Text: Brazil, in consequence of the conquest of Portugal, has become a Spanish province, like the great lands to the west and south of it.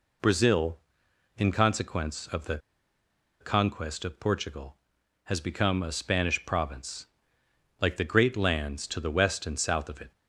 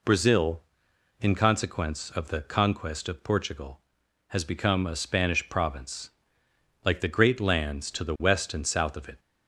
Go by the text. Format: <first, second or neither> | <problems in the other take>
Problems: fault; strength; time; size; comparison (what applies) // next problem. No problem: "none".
second | pauses between "the" and "conquest"; noticeable; at 2.5 s; 0.82 s long